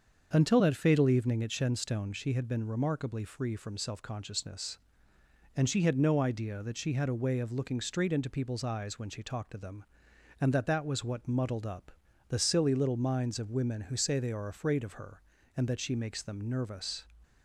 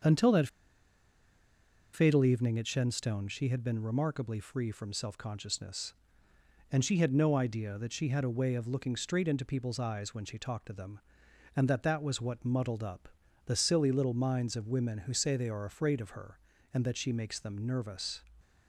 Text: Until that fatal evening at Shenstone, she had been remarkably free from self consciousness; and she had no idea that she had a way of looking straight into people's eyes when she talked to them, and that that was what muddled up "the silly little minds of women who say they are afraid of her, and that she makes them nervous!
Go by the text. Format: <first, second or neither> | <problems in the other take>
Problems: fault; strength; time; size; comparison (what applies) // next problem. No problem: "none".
first | starts louder than the rest; until 2.5 s; 7 dB; also in the first // pauses between "that" and "fatal"; strong; at 0.4 s; 1.4 s long // pauses between "up" and "the"; at 13.0 s; 0.38 s long; also in the first